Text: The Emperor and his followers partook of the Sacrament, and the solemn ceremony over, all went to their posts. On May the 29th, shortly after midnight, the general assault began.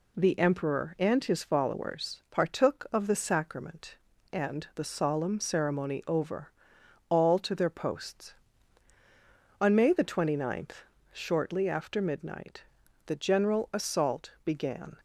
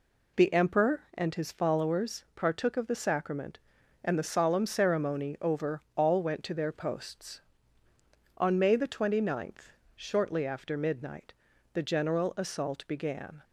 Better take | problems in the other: second | skips "went"; at 7.3 s

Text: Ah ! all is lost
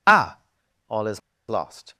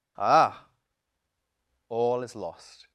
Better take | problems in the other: second | pauses between "is" and "lost"; slight; at 1.2 s; 0.29 s long

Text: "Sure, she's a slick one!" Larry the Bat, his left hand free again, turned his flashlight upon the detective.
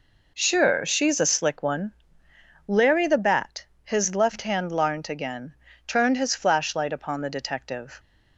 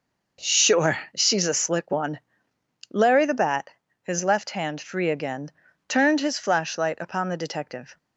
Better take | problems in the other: second | says "larnt" for "free"; at 4.7 s

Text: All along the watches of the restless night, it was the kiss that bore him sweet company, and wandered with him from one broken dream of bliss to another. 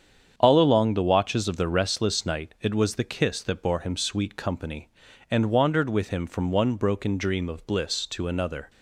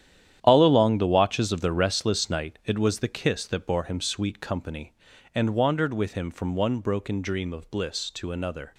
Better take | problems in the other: first | gets quieter; strong; throughout; 11 dB // starts louder than the rest; strong; until 1.4 s; 10.5 dB; strong in the first

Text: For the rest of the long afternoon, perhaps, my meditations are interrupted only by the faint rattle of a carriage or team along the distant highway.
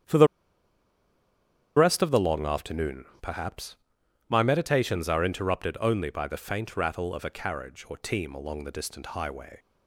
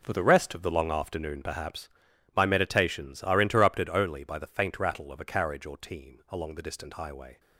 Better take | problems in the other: second | starts louder than the rest; strong; until 2.5 s; 10 dB // pauses between "the" and "rest"; strong; at 0.2 s; 1.5 s long

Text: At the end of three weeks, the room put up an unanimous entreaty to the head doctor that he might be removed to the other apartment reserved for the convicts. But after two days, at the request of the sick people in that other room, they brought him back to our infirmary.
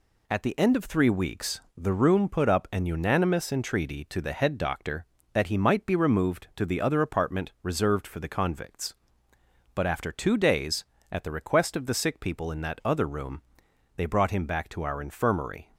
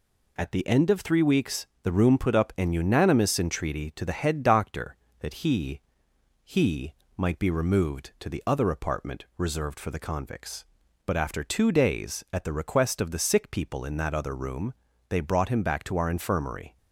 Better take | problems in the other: first | says "he" twice; at 6.4 s

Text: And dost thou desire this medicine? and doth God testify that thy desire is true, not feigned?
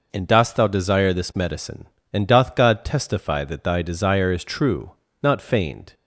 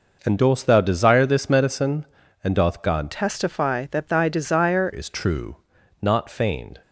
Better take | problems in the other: first | changes voice from "testify" to "desire"; from 3.1 to 4.9 s; 1.8 s long

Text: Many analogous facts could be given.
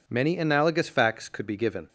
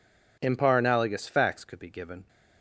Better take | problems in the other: first | says "Impar" for "Many"; at 0.3 s

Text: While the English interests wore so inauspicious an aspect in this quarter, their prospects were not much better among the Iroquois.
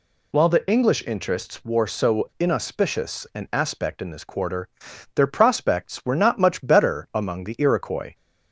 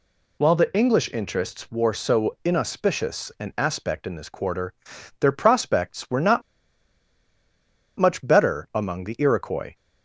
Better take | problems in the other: first | pauses between "not" and "much"; strong; at 6.4 s; 1.5 s long

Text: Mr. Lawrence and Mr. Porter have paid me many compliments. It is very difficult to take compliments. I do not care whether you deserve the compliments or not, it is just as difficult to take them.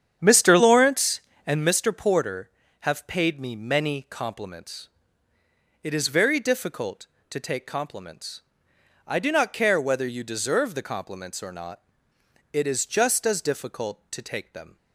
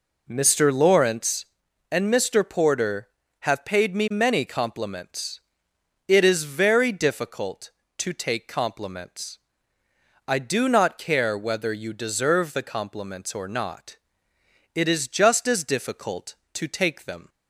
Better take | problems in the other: second | starts louder than the rest; strong; until 1.7 s; 8.5 dB

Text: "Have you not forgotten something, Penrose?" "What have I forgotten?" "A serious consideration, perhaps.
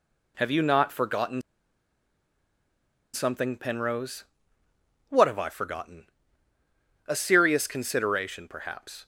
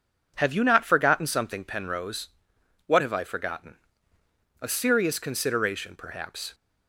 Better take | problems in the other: second | pauses between "forgotten" and "something"; strong; at 1.4 s; 1.7 s long

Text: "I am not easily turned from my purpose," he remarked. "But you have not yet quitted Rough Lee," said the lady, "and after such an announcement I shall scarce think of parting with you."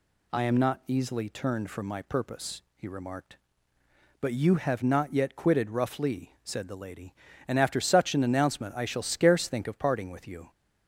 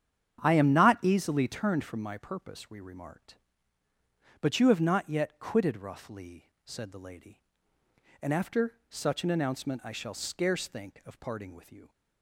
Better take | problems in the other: first | starts louder than the rest; strong; until 1.4 s; 8.5 dB // says "we" for "he"; at 2.6 s

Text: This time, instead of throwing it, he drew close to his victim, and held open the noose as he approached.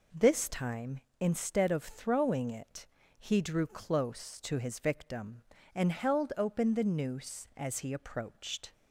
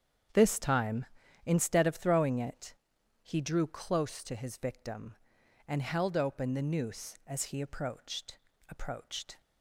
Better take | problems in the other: first | starts louder than the rest; strong; until 1.7 s; 8 dB // says "approached" twice; at 8.6 s

